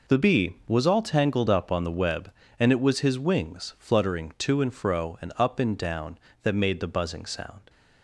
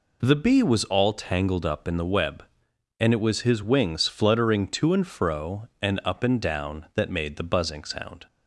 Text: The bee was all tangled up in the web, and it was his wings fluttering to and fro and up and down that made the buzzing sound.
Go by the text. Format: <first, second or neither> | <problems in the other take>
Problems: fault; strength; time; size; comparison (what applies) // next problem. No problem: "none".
second | says "on" for "in"; at 1.7 s